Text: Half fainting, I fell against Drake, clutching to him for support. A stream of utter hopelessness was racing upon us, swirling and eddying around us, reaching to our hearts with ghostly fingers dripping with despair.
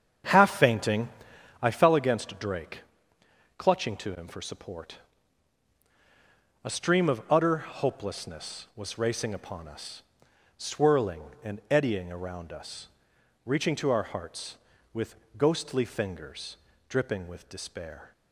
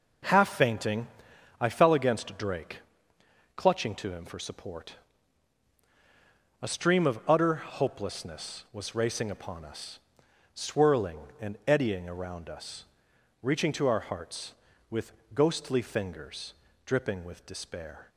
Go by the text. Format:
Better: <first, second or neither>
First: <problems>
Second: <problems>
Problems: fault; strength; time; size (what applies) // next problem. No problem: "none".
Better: second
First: starts louder than the rest; strong; until 1.9 s; 7.5 dB // pauses between "with" and "ghostly"; slight; at 15.1 s; 0.24 s long // pauses between "fingers" and "dripping"; slight; at 16.5 s; 0.32 s long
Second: pauses between "with" and "ghostly"; slight; at 15.1 s; 0.24 s long // pauses between "fingers" and "dripping"; slight; at 16.5 s; 0.32 s long